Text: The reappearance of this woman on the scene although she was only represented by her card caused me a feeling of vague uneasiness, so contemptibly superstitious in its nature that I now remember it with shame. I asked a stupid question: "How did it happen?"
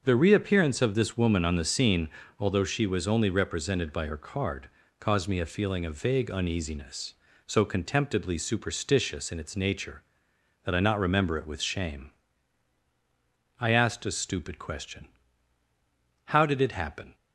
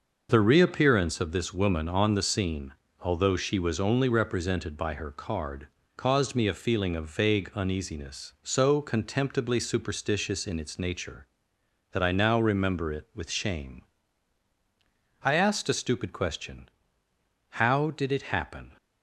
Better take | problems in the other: second | starts louder than the rest; until 1.0 s; 6 dB // pauses between "scene" and "although"; slight; at 2.0 s; 0.28 s long; slight in the second // pauses between "card" and "caused"; slight; at 4.6 s; 0.32 s long; slight in the second // says "not" for "now"; at 10.8 s

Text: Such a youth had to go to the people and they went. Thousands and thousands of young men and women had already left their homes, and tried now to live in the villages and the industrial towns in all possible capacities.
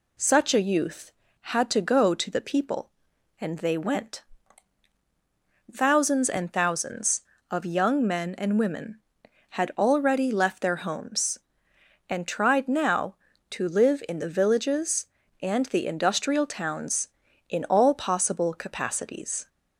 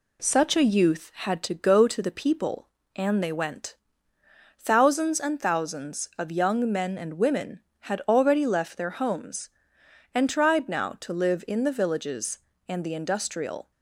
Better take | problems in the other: first | stops before "towns in all possible capacities"; at 13.7 s

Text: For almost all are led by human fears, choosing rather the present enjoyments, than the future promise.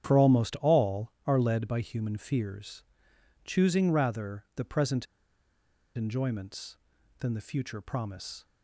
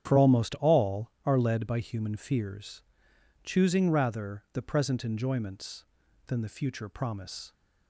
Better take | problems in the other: second | starts louder than the rest; strong; until 1.0 s; 9.5 dB; strong in the second // pauses between "present" and "enjoyments"; noticeable; at 5.0 s; 0.91 s long

